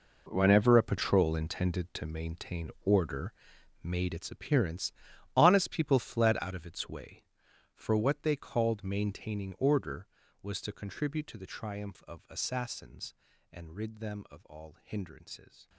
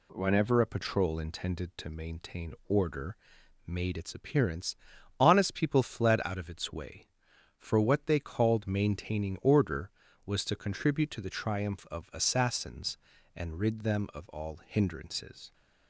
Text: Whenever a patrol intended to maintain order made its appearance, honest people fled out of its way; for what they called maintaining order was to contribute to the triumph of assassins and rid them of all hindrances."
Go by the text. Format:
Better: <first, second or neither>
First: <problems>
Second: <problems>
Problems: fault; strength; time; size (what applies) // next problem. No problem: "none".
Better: second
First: gets quieter; strong; throughout; 13.5 dB // pauses between "order" and "made"; noticeable; at 3.3 s; 0.50 s long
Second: pauses between "order" and "made"; noticeable; at 3.1 s; 0.50 s long